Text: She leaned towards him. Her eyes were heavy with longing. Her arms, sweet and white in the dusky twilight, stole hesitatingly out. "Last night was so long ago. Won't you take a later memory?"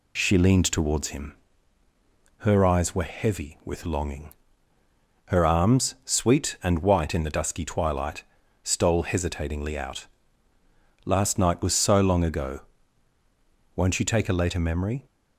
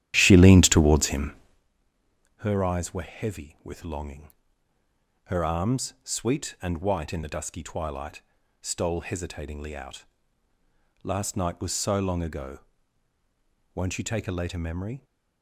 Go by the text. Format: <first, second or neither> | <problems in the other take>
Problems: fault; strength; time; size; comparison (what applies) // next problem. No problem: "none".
first | starts louder than the rest; strong; until 1.7 s; 12 dB